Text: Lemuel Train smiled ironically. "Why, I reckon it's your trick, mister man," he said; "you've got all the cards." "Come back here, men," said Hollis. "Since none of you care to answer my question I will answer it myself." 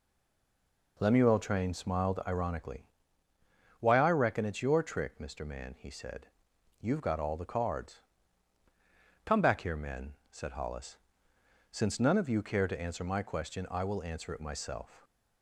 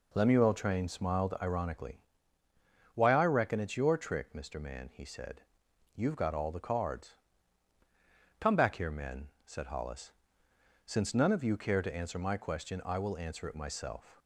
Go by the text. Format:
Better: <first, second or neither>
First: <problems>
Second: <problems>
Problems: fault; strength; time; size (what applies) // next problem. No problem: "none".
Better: second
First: stays silent before the first word; slight; until 0.9 s; 0.9 s long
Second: none